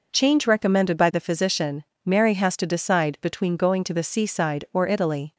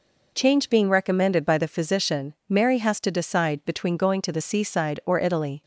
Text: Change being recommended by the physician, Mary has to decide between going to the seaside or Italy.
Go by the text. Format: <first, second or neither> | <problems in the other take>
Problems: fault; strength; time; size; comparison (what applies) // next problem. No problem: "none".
second | skips "being"; at 0.4 s